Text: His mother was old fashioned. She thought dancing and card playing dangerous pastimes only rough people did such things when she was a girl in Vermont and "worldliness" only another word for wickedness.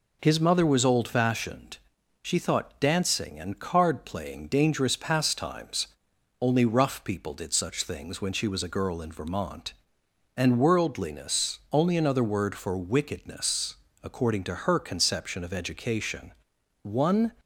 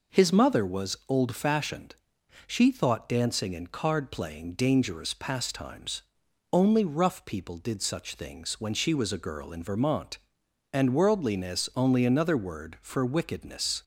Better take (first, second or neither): second